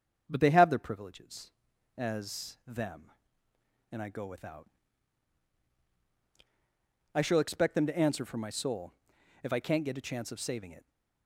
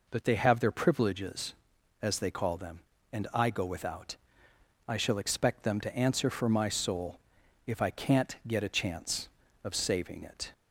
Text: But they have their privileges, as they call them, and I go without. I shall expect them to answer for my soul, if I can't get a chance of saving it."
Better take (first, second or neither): second